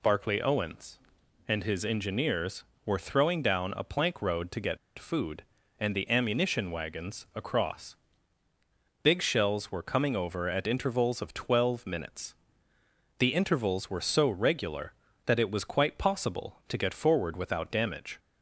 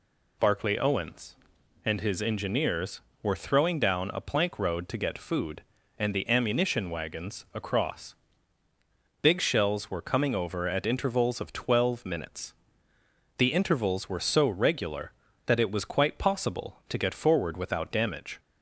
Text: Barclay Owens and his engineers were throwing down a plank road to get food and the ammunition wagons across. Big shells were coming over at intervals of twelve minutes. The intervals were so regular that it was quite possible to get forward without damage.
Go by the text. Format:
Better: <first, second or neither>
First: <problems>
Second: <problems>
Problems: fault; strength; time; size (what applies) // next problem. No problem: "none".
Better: second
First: pauses between "get" and "food"; slight; at 4.7 s; 0.20 s long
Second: none